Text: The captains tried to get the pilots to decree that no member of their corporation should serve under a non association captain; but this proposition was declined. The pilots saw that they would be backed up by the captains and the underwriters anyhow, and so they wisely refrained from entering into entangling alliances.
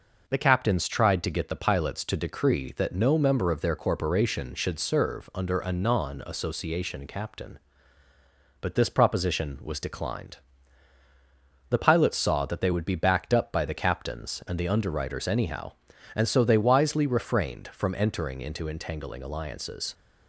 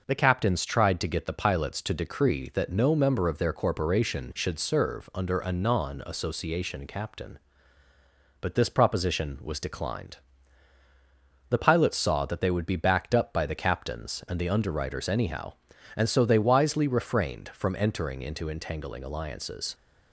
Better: neither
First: none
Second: none

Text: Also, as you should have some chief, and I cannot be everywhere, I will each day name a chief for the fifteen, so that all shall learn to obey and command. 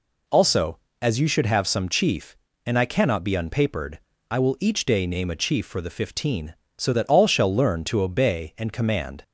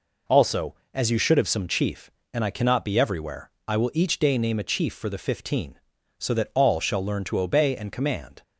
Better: second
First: says "unpapered" for "everywhere"; at 3.3 s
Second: none

